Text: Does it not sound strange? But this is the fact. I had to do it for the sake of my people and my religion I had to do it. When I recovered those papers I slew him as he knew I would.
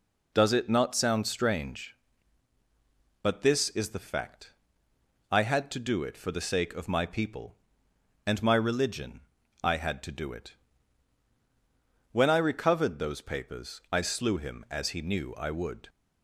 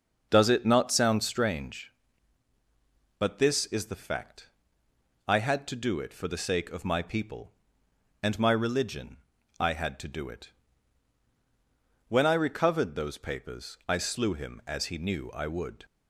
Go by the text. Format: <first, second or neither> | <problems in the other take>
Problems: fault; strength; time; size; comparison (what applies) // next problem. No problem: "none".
first | starts louder than the rest; noticeable; until 1.4 s; 6 dB // pauses between "religion" and "I"; at 9.1 s; 0.42 s long; also in the first